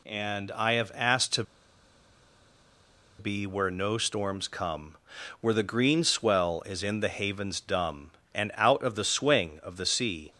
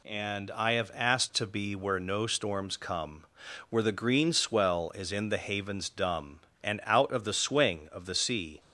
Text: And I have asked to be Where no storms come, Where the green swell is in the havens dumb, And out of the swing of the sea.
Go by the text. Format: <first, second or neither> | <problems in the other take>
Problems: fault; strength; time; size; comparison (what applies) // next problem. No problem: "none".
second | pauses between "to" and "be"; strong; at 1.4 s; 1.7 s long